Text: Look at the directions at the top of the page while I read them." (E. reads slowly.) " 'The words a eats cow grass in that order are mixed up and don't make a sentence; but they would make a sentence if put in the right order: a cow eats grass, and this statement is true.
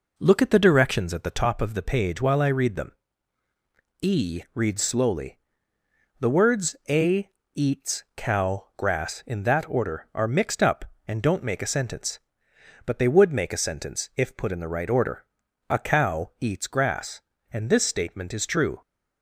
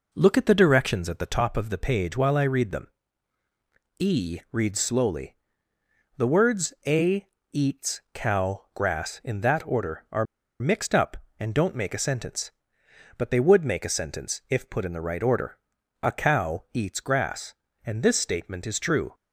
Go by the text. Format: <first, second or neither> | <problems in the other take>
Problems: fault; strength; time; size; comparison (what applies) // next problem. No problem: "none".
first | pauses between "a" and "eats"; slight; at 7.2 s; 0.28 s long; slight in the first // pauses between "are" and "mixed"; slight; at 10.2 s; 0.34 s long